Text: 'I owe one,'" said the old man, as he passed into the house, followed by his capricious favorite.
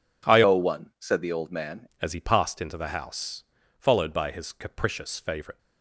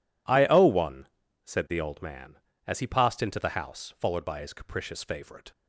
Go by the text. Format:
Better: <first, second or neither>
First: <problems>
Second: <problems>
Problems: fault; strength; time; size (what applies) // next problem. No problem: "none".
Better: second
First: changes voice from "owe" to "man"; from 0.4 to 1.8 s; 1.4 s long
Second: none